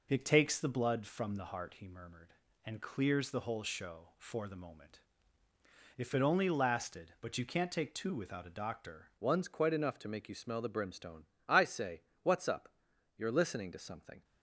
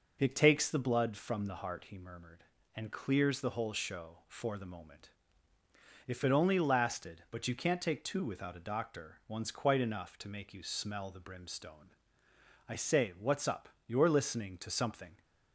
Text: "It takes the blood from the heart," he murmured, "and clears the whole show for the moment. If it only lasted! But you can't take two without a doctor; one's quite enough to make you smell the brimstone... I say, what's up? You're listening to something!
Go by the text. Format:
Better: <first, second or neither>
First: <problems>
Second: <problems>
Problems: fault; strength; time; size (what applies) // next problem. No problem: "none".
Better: second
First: changes voice at "one's"; from 9.1 s on; 5.1 s long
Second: none